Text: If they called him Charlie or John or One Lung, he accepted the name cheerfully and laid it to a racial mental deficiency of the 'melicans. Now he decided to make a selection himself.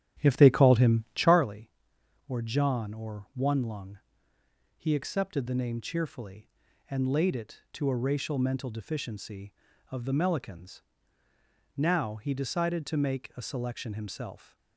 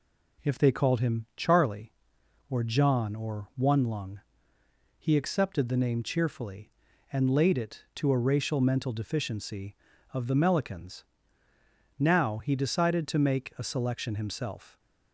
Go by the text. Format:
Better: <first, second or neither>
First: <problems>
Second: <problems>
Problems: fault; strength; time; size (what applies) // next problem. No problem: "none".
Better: second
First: starts louder than the rest; strong; until 1.4 s; 11 dB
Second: none